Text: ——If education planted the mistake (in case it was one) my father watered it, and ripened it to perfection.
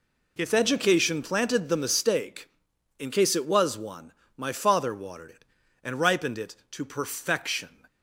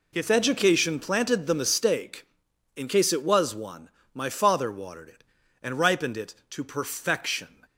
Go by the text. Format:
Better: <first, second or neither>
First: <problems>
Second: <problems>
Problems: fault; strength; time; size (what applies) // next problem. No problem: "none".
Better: neither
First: none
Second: none